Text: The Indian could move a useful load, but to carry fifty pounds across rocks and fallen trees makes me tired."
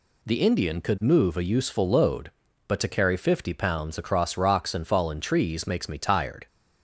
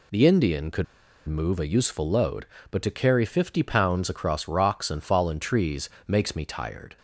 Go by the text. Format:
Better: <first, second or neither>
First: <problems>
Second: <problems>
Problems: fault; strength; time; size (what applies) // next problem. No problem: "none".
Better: first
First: none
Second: pauses between "could" and "move"; at 0.8 s; 0.43 s long // pauses between "trees" and "makes"; slight; at 5.8 s; 0.20 s long